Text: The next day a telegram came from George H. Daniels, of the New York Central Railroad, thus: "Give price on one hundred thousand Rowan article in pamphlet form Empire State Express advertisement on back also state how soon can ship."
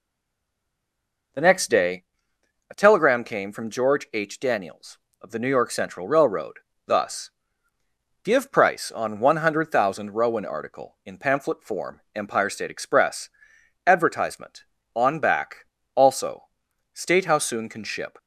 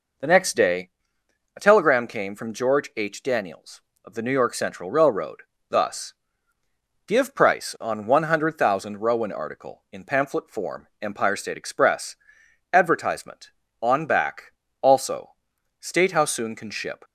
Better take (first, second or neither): second